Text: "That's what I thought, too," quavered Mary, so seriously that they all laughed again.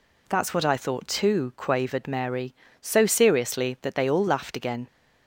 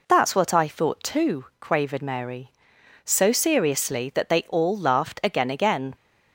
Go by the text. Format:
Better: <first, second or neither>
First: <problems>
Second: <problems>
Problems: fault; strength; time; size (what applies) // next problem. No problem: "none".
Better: first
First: none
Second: says "again" twice; at 5.4 s